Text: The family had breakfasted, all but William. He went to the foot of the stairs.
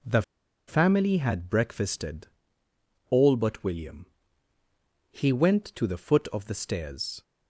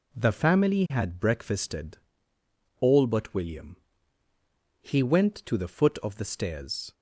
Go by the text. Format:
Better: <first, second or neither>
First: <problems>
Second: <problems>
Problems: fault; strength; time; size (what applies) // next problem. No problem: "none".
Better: second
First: pauses between "The" and "family"; noticeable; at 0.2 s; 0.46 s long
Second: none